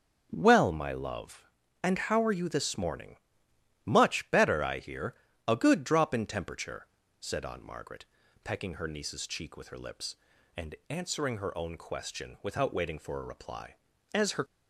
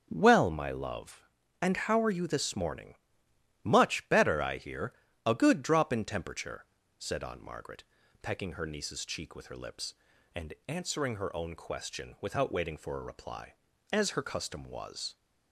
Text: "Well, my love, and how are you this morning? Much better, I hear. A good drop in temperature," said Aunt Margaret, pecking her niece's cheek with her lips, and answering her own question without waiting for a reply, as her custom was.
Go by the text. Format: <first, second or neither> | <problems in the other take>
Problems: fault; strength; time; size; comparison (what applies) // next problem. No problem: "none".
second | stops before "custom was"; at 14.4 s